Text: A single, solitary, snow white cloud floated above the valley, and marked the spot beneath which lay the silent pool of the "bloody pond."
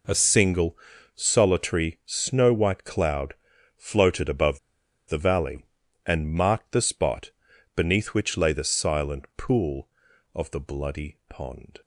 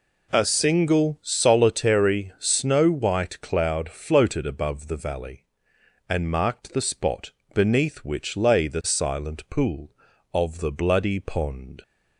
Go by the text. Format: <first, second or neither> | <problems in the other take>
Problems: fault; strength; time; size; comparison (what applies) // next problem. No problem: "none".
second | pauses between "cloud" and "floated"; at 3.3 s; 0.42 s long // pauses between "above" and "the"; noticeable; at 4.5 s; 0.49 s long // pauses between "spot" and "beneath"; at 7.3 s; 0.44 s long; slight in the second